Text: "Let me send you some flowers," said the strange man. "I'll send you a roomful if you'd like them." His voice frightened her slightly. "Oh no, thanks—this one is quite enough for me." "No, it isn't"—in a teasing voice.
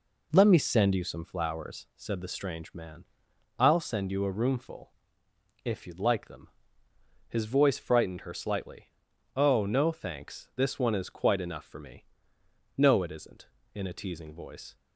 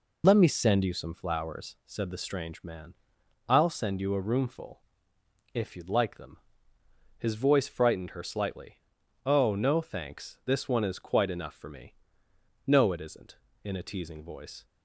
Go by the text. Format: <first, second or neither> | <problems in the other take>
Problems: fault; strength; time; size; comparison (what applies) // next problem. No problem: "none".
first | loses the start of "Let"; at 0.2 s; 25 ms // pauses between "roomful" and "if"; noticeable; at 4.8 s; 0.72 s long; noticeable in the first